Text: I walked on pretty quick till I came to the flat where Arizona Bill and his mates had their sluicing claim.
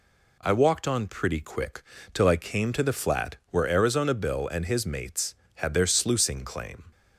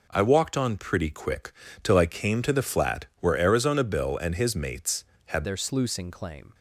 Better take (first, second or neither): first